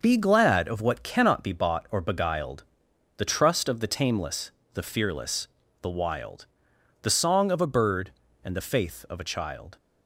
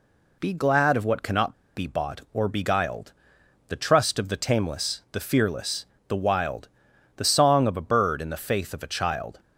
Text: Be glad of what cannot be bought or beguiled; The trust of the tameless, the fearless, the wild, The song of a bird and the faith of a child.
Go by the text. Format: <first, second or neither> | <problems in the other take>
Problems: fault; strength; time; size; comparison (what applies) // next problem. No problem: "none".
first | pauses between "cannot" and "be"; slight; at 1.5 s; 0.21 s long